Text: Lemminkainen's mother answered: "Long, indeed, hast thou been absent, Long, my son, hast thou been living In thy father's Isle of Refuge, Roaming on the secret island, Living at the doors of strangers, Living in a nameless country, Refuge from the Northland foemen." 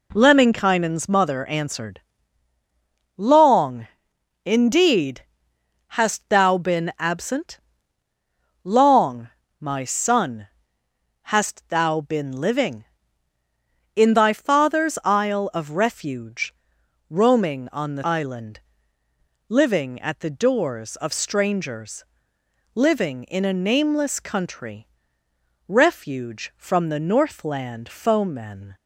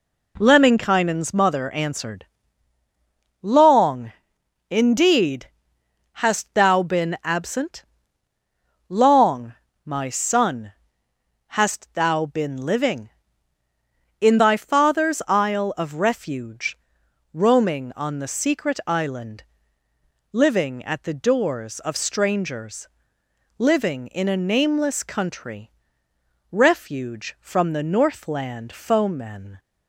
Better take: second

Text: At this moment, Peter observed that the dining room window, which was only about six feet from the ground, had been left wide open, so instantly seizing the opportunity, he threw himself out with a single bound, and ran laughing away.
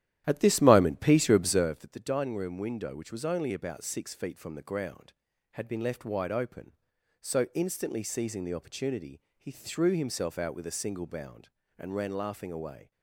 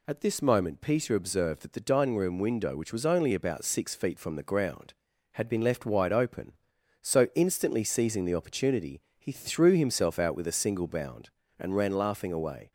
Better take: second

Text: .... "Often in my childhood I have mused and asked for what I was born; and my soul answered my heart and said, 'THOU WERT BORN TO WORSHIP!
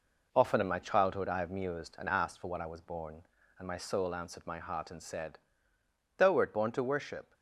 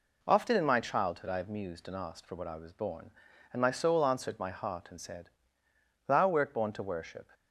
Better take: second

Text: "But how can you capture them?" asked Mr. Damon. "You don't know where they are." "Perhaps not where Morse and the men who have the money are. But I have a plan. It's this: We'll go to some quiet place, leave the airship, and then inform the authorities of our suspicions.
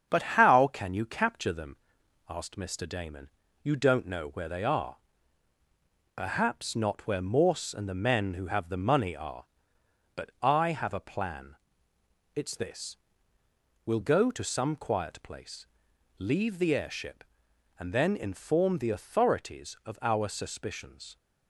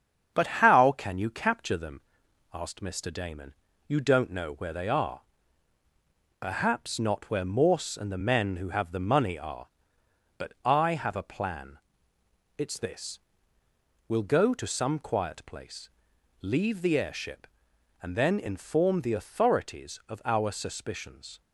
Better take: neither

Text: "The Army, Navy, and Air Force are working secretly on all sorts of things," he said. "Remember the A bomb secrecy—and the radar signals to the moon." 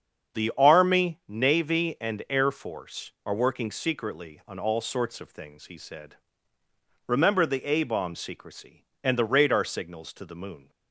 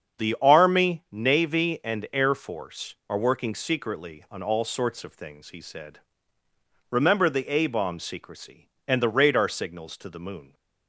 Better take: neither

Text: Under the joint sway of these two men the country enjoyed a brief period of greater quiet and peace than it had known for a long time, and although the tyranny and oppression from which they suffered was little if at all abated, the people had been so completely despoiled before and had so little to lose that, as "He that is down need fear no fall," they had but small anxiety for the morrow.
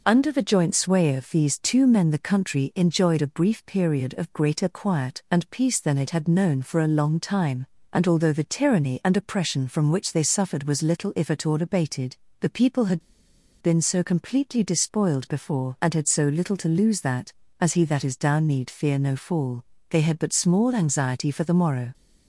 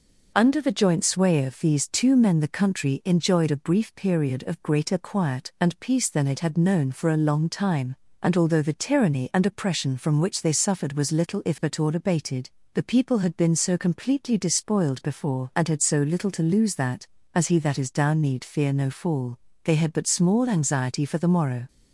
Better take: second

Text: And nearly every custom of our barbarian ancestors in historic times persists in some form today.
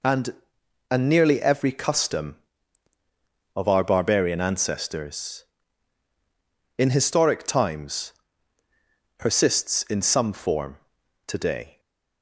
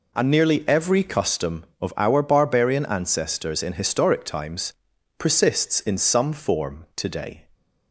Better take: second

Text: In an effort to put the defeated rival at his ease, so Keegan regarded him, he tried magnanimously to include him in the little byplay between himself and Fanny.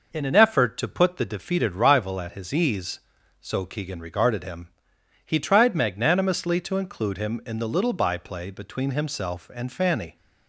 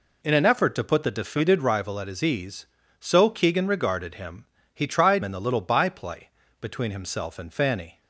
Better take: first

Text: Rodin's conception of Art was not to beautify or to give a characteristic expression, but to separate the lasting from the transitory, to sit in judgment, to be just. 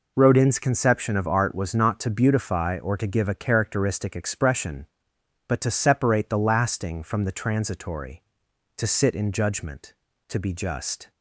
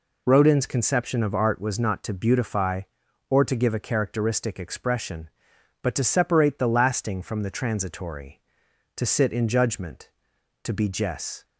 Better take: first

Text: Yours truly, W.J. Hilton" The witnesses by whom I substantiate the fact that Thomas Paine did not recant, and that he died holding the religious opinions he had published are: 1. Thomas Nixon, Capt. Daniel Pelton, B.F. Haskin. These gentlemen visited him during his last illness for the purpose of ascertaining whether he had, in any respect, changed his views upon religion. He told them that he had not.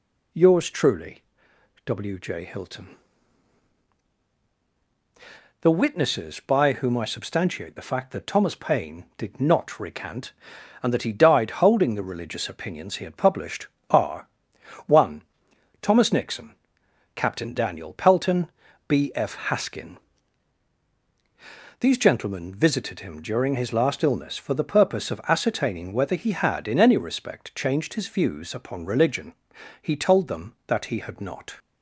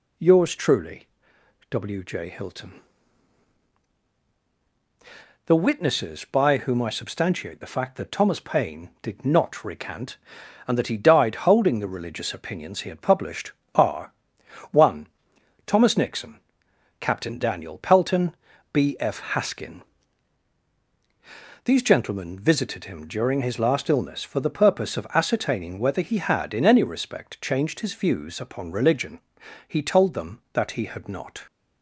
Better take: neither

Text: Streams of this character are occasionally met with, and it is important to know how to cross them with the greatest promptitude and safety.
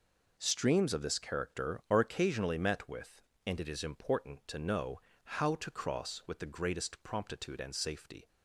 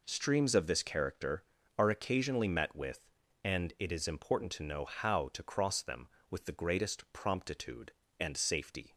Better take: second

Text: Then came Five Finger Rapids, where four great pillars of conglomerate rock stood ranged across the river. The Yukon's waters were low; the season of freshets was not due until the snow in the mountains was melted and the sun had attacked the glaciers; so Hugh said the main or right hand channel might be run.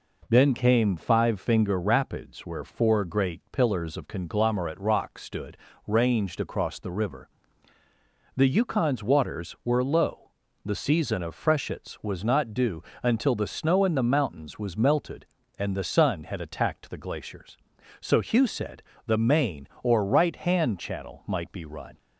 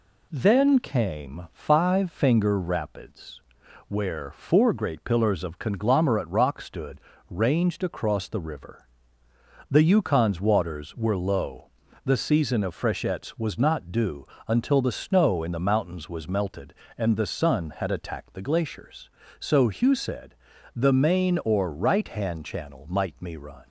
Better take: first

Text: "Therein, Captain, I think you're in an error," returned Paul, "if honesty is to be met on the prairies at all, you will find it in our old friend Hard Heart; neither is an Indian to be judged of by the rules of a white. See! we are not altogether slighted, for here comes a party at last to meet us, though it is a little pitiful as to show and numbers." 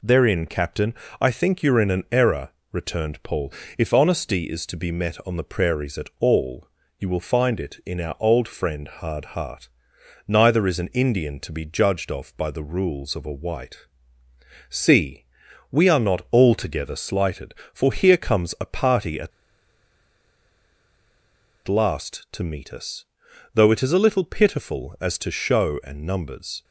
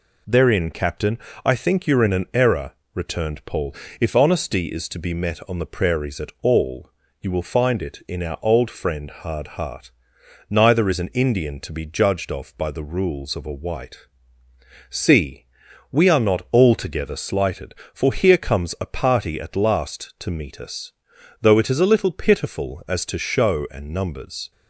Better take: second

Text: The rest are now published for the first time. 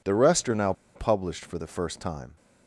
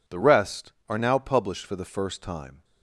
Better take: second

